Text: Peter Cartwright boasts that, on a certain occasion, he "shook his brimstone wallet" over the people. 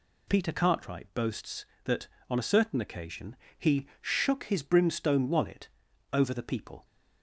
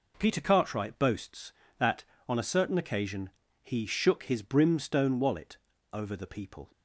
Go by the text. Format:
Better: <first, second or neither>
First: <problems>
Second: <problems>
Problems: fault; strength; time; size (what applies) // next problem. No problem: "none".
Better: neither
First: pauses between "wallet" and "over"; at 5.6 s; 0.44 s long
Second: pauses between "wallet" and "over"; slight; at 5.5 s; 0.34 s long